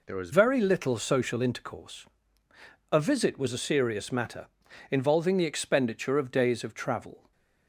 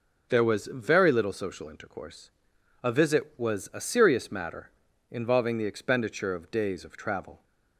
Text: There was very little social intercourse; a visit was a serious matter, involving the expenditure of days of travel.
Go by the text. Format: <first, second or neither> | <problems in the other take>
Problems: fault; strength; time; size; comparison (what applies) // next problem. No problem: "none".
second | changes voice at "very"; from 0.3 s on; 7.0 s long // stays silent after the last word; slight; from 7.1 s on; 0.5 s long